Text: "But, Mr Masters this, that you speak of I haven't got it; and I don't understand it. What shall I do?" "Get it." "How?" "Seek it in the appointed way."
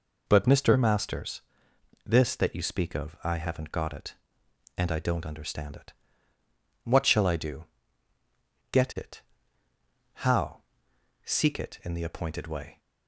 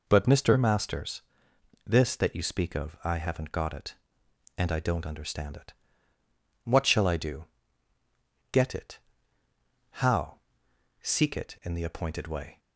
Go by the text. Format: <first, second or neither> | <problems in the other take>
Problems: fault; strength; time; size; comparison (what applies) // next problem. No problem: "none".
neither | pauses between "Masters" and "this"; noticeable; the same in both